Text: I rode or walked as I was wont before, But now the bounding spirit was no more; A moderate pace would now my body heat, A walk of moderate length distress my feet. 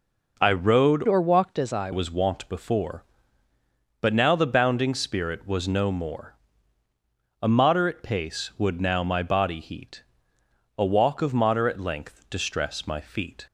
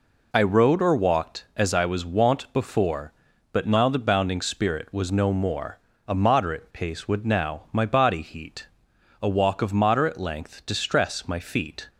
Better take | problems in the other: second | changes voice from "or" to "I"; from 1.0 to 1.9 s; 0.9 s long

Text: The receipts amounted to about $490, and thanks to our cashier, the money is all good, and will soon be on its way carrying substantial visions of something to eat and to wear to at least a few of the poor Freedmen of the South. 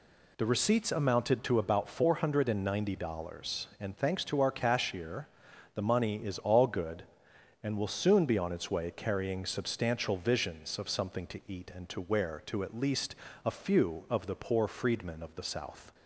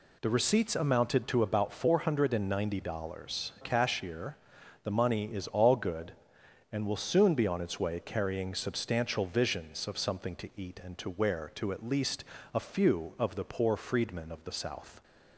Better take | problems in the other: first | skips "and thanks to our"; at 3.5 s // pauses between "least" and "a"; slight; at 12.2 s; 0.32 s long; slight in the first

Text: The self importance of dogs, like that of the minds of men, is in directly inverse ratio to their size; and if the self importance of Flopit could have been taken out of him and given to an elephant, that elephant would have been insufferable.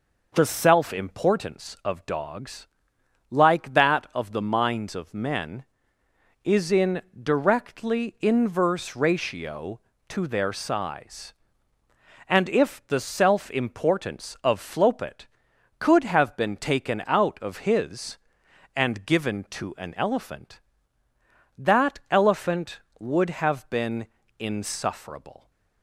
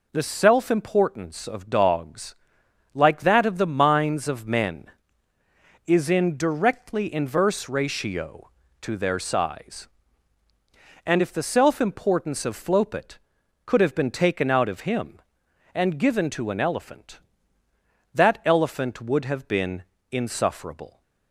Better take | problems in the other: second | pauses between "in" and "directly"; slight; at 7.0 s; 0.18 s long // says "his" for "him"; at 17.5 s // pauses between "been" and "insufferable"; slight; at 24.0 s; 0.32 s long; slight in the second

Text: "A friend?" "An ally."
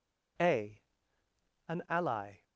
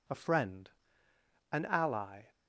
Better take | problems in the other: second | skips "friend"; at 1.2 s

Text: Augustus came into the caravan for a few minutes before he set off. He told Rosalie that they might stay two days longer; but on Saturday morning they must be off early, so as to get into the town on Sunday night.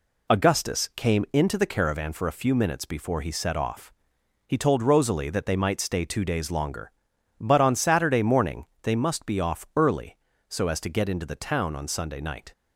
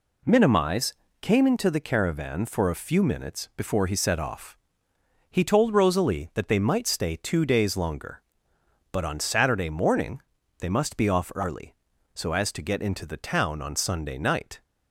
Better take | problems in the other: first | says "Minimize" for "Augustus"; at 0.2 s // pauses between "morning" and "they"; at 10.2 s; 0.38 s long; slight in the first

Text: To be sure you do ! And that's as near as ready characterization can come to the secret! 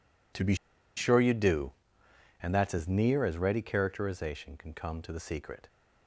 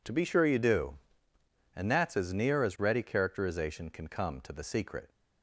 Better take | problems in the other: second | pauses between "be" and "sure"; at 0.5 s; 0.41 s long

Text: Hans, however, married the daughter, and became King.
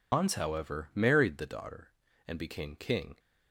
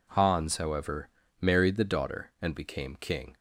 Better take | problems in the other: second | loses the start of "Hans"; at 0.1 s; 105 ms

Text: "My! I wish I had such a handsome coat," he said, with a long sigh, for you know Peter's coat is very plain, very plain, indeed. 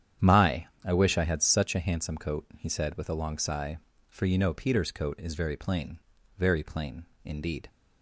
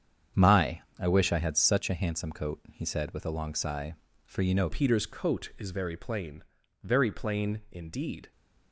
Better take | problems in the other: first | starts louder than the rest; strong; until 1.5 s; 8 dB; strong in the first // changes voice at "Peter's"; from 4.6 s on; 3.7 s long

